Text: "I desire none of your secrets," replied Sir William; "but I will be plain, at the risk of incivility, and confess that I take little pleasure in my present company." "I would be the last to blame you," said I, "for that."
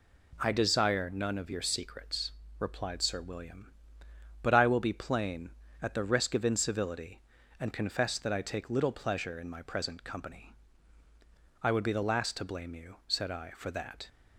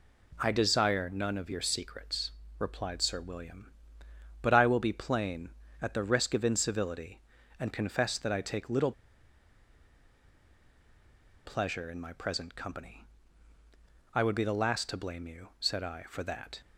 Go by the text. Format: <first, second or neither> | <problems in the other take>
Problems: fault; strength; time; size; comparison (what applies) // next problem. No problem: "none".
first | pauses between "little" and "pleasure"; strong; at 8.9 s; 2.5 s long